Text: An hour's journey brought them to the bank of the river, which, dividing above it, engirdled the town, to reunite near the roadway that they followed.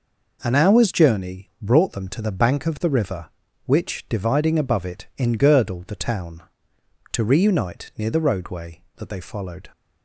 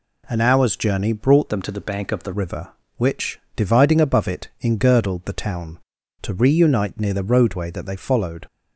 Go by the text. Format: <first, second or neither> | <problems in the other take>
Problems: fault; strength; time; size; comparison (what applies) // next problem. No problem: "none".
first | changes voice from "them" to "the"; from 1.4 to 2.3 s; 0.9 s long